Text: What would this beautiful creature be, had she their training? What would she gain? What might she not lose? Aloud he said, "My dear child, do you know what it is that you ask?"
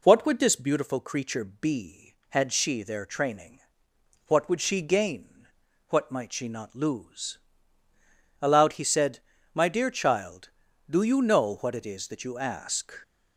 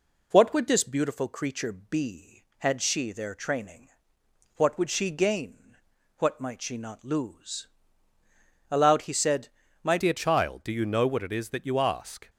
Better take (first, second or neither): first